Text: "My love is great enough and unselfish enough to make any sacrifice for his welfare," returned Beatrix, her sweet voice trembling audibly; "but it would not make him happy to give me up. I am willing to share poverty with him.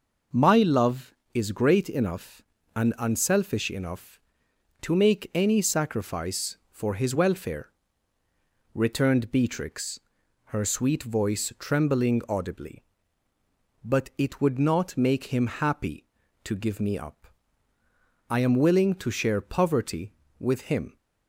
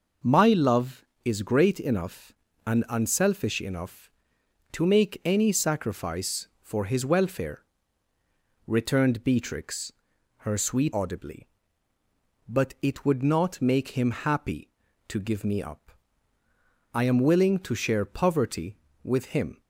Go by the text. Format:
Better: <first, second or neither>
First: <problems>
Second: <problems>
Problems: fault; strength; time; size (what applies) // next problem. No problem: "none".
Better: first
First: none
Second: skips "voice trembling"; at 10.9 s